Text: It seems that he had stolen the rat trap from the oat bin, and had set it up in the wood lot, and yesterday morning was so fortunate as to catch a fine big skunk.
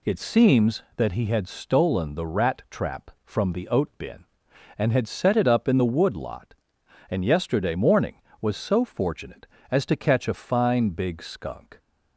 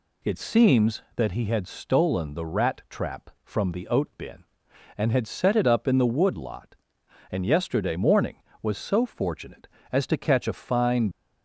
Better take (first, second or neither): first